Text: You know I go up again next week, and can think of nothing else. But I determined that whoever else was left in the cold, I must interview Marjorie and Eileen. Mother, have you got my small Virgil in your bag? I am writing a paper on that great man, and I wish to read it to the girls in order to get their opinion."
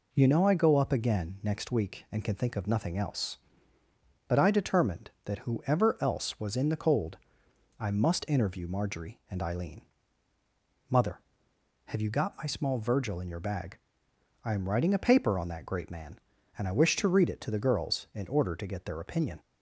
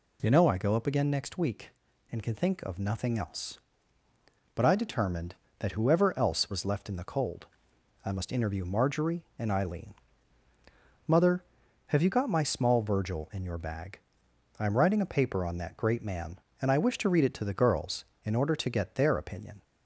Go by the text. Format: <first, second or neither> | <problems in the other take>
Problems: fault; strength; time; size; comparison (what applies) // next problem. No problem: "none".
second | skips "left"; at 6.5 s